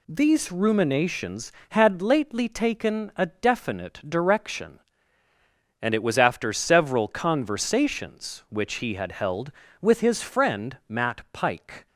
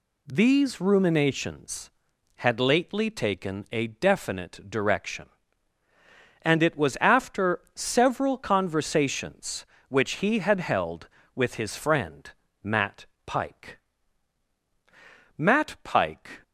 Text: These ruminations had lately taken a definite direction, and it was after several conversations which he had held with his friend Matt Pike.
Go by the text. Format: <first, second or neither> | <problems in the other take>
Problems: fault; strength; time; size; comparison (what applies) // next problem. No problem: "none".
first | pauses between "after" and "several"; slight; at 7.6 s; 0.16 s long // pauses between "friend" and "Matt"; slight; at 12.3 s; 0.30 s long // pauses between "Matt" and "Pike"; slight; at 13.0 s; 0.20 s long // goes on to say "Matt Pike"; noticeable; from 15.3 s on; 1.0 s long